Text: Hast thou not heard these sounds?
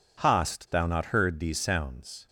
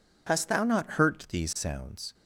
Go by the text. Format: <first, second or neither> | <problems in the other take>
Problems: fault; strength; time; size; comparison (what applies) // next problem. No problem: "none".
first | says "hurt" for "heard"; at 0.8 s